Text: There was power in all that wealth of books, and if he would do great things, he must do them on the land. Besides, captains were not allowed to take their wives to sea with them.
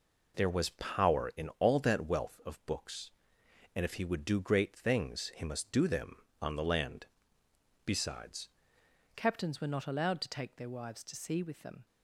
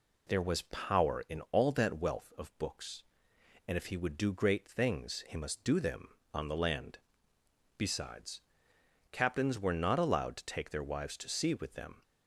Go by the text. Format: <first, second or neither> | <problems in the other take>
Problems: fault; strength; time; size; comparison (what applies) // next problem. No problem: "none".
second | changes voice at "captains"; from 9.1 s on; 2.7 s long